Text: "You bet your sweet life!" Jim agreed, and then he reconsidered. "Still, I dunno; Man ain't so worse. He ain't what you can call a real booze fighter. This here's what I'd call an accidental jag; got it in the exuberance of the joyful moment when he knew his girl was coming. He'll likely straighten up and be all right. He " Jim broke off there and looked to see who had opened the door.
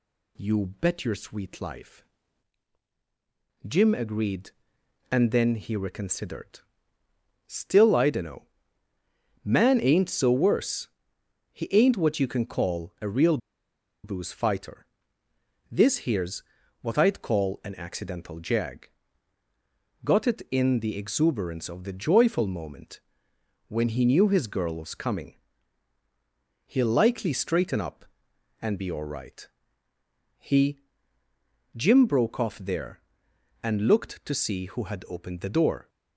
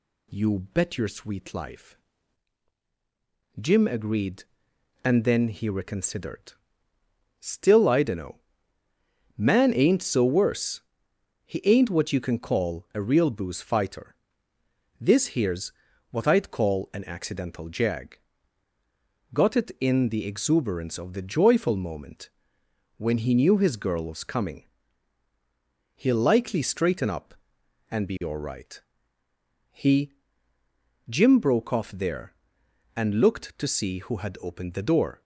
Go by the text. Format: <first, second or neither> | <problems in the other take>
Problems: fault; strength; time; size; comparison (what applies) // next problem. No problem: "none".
second | pauses between "real" and "booze"; noticeable; at 13.3 s; 0.66 s long // pauses between "here's" and "what"; at 16.4 s; 0.38 s long; also in the second // pauses between "moment" and "when"; noticeable; at 23.0 s; 0.68 s long; noticeable in the second